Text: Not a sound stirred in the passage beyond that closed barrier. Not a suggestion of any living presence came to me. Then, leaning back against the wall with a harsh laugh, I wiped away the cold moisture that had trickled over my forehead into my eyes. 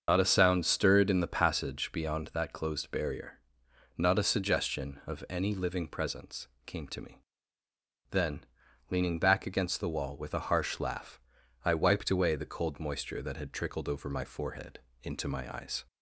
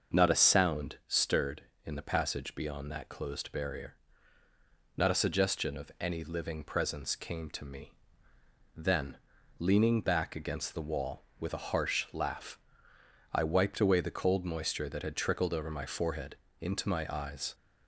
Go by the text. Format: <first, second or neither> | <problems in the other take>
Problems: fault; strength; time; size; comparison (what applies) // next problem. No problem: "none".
second | loses the start of "Not"; at 0.0 s; 55 ms // starts louder than the rest; until 1.0 s; 7 dB; also in the second // pauses between "presence" and "came"; slight; at 6.4 s; 0.20 s long // pauses between "forehead" and "into"; slight; at 14.7 s; 0.24 s long; slight in the second